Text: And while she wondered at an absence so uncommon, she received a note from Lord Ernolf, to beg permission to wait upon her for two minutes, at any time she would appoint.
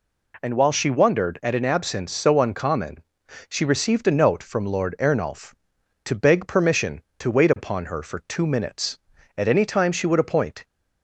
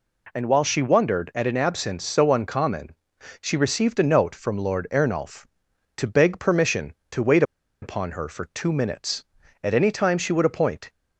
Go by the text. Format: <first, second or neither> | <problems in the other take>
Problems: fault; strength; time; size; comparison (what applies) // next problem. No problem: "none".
first | pauses between "wait" and "upon"; at 7.4 s; 0.38 s long